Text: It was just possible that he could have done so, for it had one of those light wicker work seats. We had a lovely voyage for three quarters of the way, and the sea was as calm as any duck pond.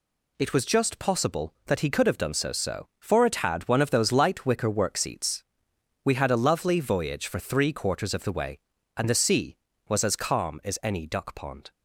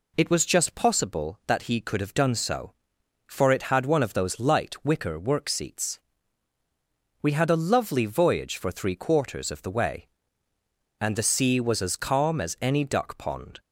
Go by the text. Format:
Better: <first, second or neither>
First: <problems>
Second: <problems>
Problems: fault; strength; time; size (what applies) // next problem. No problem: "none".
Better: second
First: says "so" twice; at 2.5 s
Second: none